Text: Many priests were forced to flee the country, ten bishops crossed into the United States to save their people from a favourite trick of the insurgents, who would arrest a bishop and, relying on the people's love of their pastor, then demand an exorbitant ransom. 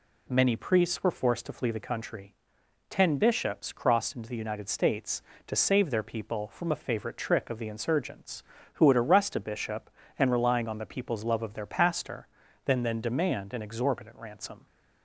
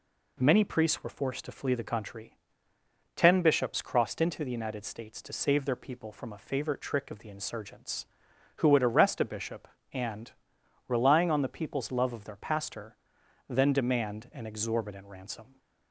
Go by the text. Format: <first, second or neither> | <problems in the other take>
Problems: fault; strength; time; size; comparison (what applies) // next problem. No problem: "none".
second | says "then" twice; at 12.8 s